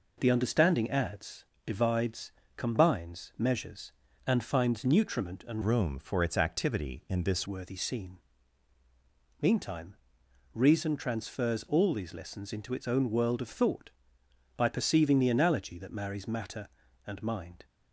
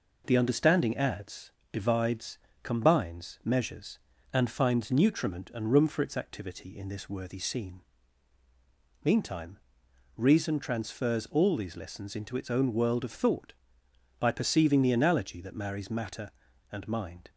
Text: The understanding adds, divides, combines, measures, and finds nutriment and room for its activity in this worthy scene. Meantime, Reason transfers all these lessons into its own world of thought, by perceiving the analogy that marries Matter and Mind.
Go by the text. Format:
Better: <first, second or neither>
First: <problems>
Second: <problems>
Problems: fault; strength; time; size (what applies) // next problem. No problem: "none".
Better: second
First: changes voice from "room" to "this"; from 5.6 to 7.4 s; 1.8 s long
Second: none